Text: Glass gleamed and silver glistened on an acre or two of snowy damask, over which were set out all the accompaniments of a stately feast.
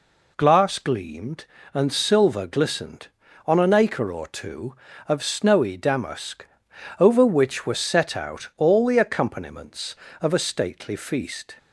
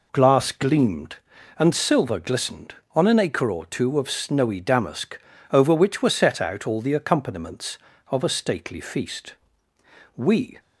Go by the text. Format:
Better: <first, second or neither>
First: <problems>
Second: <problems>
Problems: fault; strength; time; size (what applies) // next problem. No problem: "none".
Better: first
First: none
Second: goes on to say "We"; slight; from 10.1 s on; 0.44 s long